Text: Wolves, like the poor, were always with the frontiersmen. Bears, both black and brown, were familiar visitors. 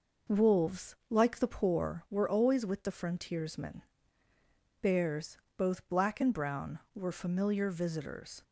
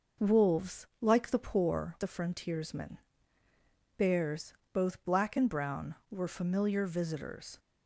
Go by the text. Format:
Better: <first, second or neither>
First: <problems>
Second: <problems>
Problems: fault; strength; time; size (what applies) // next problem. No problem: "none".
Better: first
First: none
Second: skips "were always with"; at 1.9 s